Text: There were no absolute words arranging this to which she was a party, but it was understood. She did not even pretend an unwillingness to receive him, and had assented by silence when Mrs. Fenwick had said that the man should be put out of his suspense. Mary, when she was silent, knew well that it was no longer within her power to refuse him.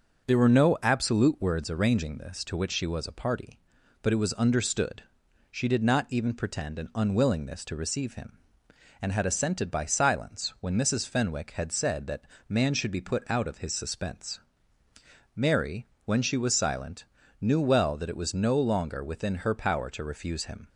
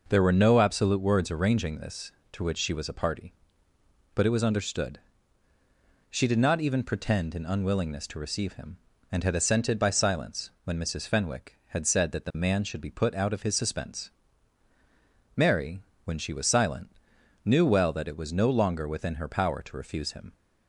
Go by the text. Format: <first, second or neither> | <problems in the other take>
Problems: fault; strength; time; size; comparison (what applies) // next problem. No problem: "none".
second | starts louder than the rest; until 1.3 s; 6.5 dB // skips "the"; at 12.3 s